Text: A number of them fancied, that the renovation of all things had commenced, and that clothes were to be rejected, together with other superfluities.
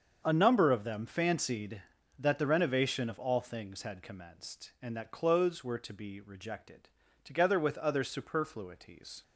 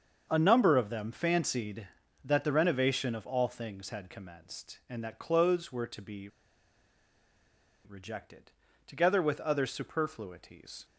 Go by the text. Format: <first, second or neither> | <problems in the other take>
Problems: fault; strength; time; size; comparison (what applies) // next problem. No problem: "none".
first | starts louder than the rest; until 1.3 s; 7 dB; also in the first // pauses between "be" and "rejected"; strong; at 6.2 s; 1.5 s long